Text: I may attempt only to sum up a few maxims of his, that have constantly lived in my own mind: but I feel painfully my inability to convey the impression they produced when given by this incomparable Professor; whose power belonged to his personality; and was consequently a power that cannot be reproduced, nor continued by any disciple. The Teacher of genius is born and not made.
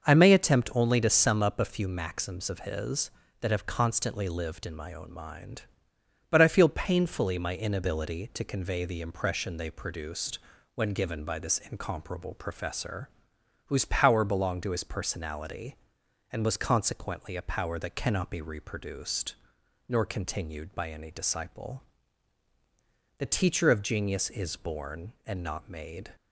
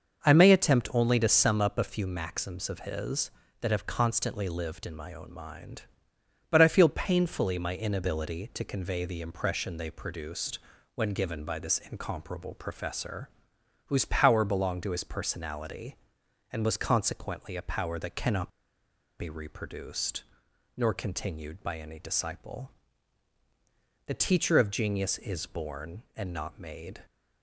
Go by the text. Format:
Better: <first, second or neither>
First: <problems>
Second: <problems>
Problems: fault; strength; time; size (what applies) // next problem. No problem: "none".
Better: first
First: starts louder than the rest; until 1.0 s; 6 dB // pauses between "produced" and "when"; slight; at 10.3 s; 0.34 s long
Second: starts louder than the rest; until 1.2 s; 6 dB // pauses between "produced" and "when"; slight; at 10.5 s; 0.34 s long // pauses between "cannot" and "be"; noticeable; at 18.5 s; 0.68 s long